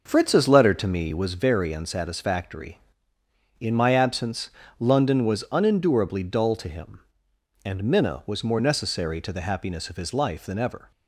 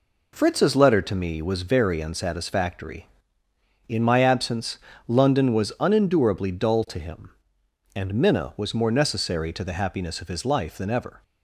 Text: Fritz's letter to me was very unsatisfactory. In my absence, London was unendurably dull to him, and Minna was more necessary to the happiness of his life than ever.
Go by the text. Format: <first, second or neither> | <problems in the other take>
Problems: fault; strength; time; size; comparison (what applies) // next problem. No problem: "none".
second | starts louder than the rest; noticeable; until 1.3 s; 6 dB